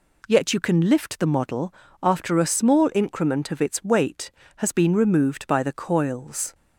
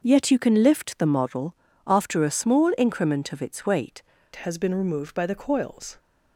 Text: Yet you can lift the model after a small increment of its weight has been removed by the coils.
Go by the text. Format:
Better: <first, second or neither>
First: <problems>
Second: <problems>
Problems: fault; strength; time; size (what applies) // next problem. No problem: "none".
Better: first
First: pauses between "model" and "after"; slight; at 1.7 s; 0.28 s long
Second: starts louder than the rest; until 1.0 s; 6 dB // pauses between "model" and "after"; slight; at 1.5 s; 0.32 s long // changes voice at "has"; from 4.3 s on; 1.6 s long